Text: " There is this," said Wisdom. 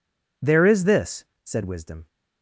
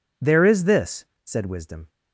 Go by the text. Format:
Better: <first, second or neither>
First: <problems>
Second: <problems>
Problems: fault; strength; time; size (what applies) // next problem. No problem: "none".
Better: neither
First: none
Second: none